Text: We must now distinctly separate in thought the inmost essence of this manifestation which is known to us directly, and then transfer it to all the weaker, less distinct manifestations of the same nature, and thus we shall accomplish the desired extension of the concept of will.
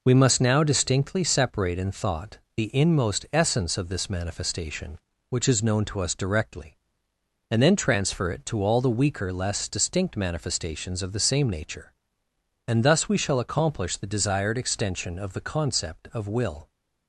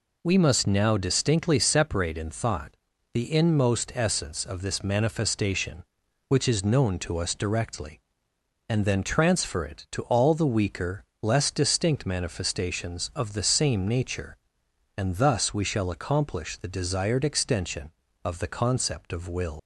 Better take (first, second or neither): first